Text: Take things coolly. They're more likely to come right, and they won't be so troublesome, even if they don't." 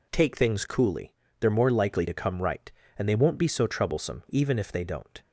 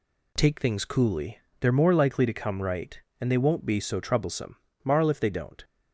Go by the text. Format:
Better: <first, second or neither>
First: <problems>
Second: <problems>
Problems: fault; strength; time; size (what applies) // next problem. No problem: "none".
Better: first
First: none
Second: says "marl" for "even"; at 4.8 s